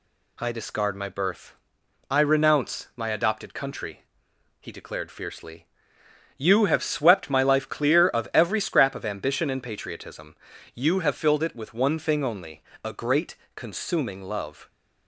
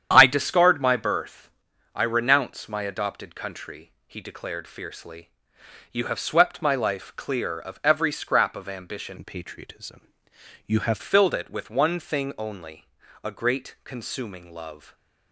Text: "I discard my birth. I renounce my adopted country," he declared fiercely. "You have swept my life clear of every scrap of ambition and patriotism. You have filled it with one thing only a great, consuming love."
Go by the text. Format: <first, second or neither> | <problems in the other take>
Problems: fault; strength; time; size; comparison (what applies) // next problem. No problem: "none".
first | starts louder than the rest; strong; until 1.1 s; 9 dB // changes voice from "and" to "have"; from 9.1 to 10.9 s; 1.8 s long // pauses between "only" and "a"; at 12.8 s; 0.38 s long; slight in the first